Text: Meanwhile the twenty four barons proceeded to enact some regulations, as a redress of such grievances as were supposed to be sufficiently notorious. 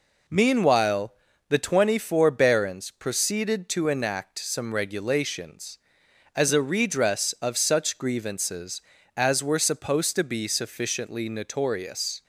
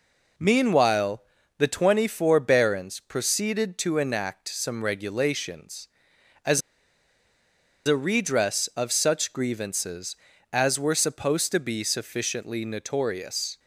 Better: first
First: pauses between "Meanwhile" and "the"; slight; at 1.1 s; 0.36 s long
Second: pauses between "Meanwhile" and "the"; slight; at 1.2 s; 0.36 s long // pauses between "as" and "a"; strong; at 6.6 s; 1.2 s long

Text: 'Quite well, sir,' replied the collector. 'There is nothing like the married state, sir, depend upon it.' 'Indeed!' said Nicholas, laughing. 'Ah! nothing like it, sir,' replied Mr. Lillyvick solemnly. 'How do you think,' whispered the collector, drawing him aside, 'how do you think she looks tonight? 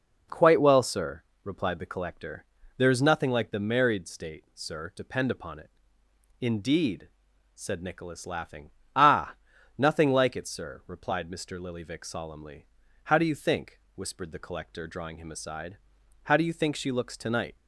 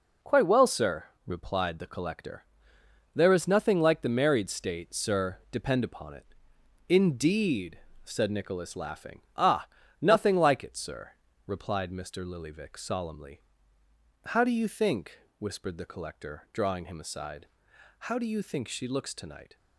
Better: neither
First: none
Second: none

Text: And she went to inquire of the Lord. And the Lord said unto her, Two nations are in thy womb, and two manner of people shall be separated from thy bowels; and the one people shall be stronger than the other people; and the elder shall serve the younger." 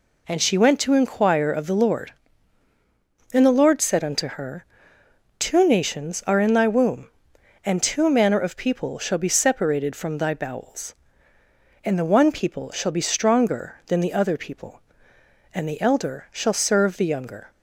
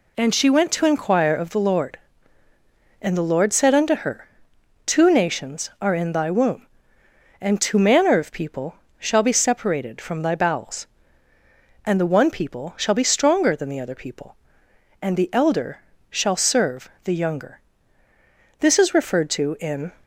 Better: first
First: none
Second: pauses between "people" and "shall"; slight; at 8.7 s; 0.24 s long // pauses between "elder" and "shall"; slight; at 15.7 s; 0.32 s long // pauses between "serve" and "the"; slight; at 16.8 s; 0.16 s long // goes on to say "This is referred to in"; from 18.5 s on; 1.3 s long

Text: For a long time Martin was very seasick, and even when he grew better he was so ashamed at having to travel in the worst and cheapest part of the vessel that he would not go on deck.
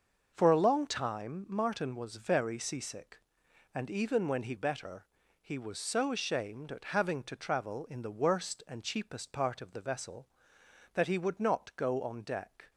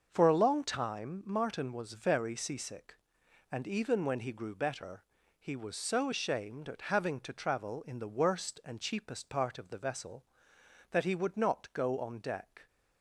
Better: second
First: starts louder than the rest; until 1.3 s; 6.5 dB // skips "grew"; at 4.5 s // pauses between "better" and "he"; slight; at 5.0 s; 0.34 s long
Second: starts louder than the rest; until 1.1 s; 6.5 dB // pauses between "better" and "he"; slight; at 5.0 s; 0.34 s long

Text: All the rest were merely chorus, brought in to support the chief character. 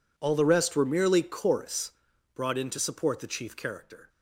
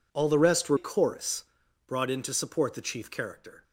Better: first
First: none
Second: skips "merely"; at 0.7 s

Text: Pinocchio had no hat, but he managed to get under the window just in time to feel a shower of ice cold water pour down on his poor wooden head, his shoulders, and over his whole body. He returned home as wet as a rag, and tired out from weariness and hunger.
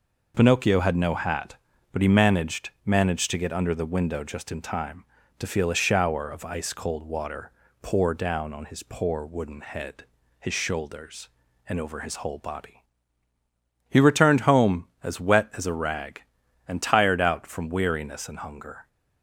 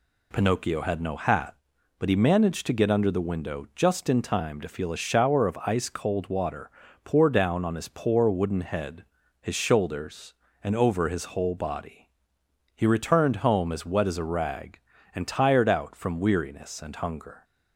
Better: second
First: says "managed" twice; at 2.8 s // pauses between "water" and "pour"; slight; at 7.5 s; 0.30 s long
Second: pauses between "water" and "pour"; slight; at 6.6 s; 0.34 s long

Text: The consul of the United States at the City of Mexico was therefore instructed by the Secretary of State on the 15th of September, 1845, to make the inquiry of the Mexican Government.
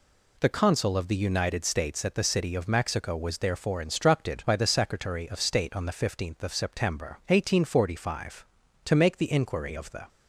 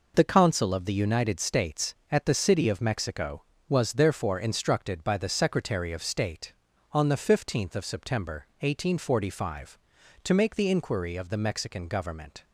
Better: second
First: stops before "Mexican Government"; at 10.0 s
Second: none

